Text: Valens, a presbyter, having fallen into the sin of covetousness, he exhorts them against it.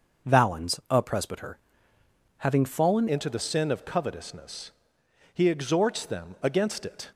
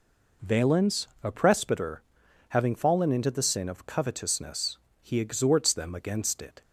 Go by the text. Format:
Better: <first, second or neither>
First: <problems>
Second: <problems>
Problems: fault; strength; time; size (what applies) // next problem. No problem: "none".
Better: second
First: starts louder than the rest; noticeable; until 1.3 s; 6 dB // changes voice at "into"; from 3.0 s on; 4.1 s long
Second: none